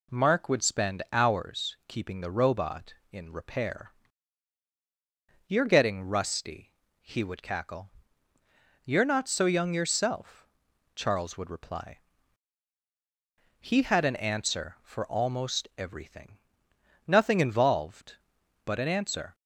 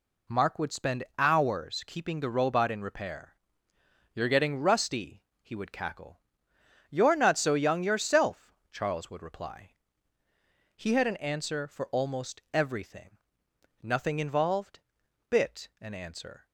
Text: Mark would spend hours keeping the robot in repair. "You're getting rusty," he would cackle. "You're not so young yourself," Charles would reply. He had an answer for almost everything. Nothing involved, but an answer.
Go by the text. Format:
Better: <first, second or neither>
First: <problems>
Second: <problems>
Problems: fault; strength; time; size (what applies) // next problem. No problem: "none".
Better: first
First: none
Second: says "bit" for "but"; at 15.2 s